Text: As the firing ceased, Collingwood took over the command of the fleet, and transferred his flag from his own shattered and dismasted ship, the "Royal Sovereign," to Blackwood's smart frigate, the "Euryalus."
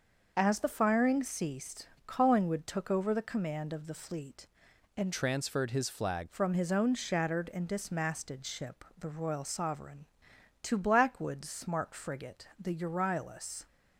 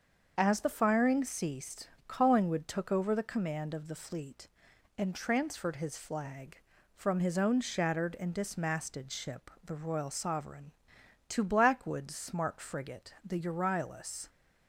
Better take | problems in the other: second | starts louder than the rest; until 1.3 s; 6.5 dB; also in the second // changes voice from "transferred" to "flag"; from 5.1 to 6.2 s; 1.1 s long

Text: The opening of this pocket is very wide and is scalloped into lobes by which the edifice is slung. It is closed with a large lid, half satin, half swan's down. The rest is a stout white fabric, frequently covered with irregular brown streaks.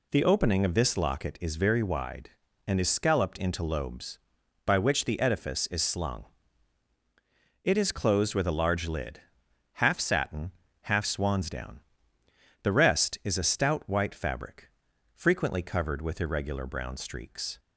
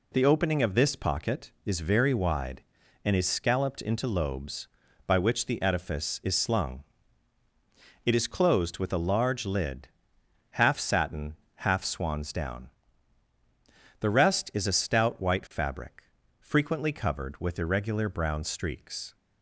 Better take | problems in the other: second | says "locket" for "pocket"; at 0.9 s

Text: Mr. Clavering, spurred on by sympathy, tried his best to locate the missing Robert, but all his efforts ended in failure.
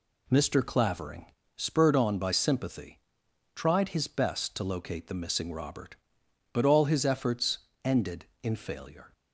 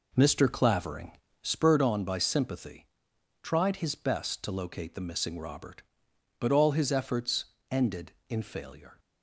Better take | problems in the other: first | starts louder than the rest; noticeable; until 1.8 s; 4 dB // pauses between "efforts" and "ended"; slight; at 7.4 s; 0.26 s long; slight in the first

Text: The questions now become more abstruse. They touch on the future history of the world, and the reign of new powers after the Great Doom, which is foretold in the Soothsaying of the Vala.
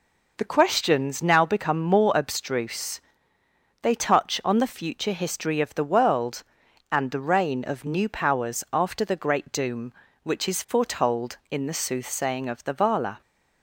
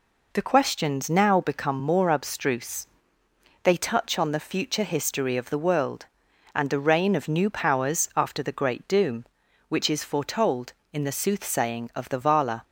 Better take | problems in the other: neither | none

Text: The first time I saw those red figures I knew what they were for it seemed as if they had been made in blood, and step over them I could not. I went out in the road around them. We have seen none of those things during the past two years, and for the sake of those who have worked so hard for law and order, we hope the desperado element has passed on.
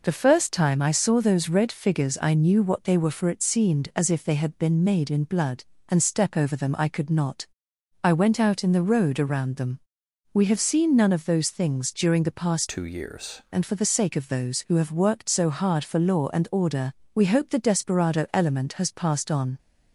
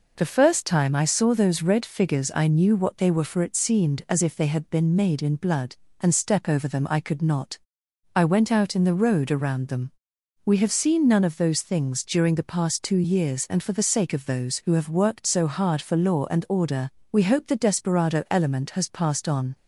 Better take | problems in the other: second | changes voice from "two" to "years"; from 12.6 to 13.4 s; 0.8 s long

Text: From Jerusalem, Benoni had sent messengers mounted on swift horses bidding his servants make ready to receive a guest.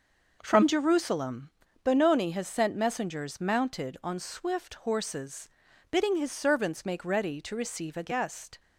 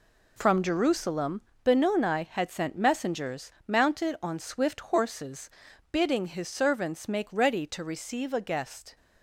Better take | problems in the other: second | says "has" for "had"; at 2.3 s // pauses between "horses" and "bidding"; at 5.4 s; 0.40 s long; also in the second

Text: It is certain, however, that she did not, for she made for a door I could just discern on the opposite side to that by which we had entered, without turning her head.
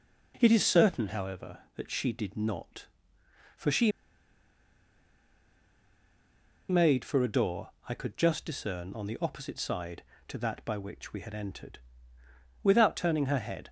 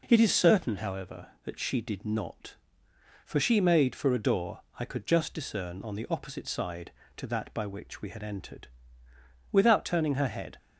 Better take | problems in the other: second | pauses between "she" and "made"; strong; at 3.9 s; 2.7 s long // pauses between "door" and "I"; slight; at 7.6 s; 0.18 s long; slight in the second

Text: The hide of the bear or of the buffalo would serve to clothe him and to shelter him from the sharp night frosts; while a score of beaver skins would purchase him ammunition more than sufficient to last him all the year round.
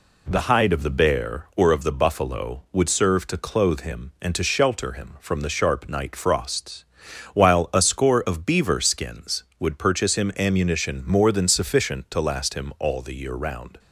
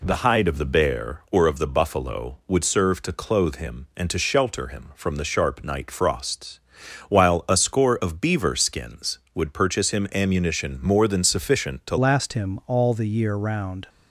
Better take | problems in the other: first | changes voice at "last"; from 11.9 s on; 1.9 s long

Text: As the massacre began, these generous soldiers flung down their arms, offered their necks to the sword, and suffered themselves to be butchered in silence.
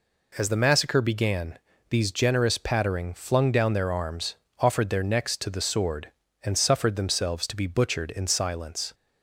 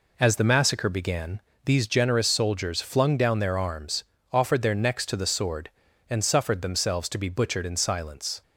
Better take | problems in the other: second | says "pattering" for "soldiers"; at 2.5 s

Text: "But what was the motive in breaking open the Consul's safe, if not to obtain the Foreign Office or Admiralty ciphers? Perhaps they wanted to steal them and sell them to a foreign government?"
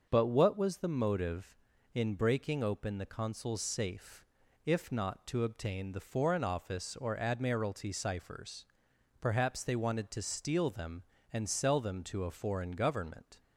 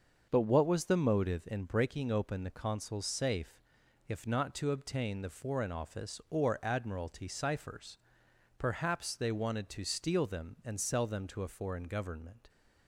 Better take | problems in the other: neither | starts louder than the rest; the same in both

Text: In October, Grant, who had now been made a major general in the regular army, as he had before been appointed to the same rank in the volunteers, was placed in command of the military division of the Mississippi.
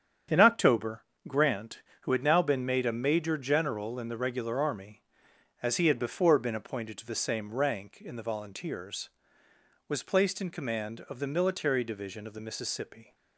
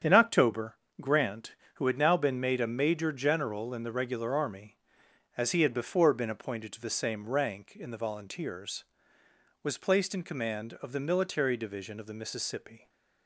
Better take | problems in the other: neither | starts louder than the rest; strong; the same in both

